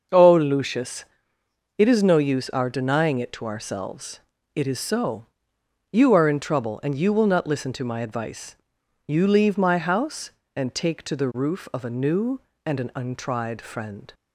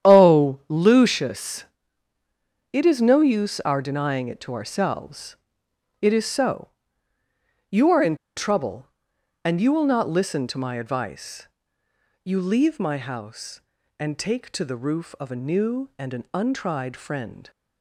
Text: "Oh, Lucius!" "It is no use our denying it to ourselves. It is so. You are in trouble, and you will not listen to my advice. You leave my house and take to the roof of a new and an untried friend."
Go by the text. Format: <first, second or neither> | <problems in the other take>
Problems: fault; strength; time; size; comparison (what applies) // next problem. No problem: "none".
first | starts louder than the rest; strong; until 1.1 s; 10 dB; also in the first // pauses between "in" and "trouble"; slight; at 8.1 s; 0.19 s long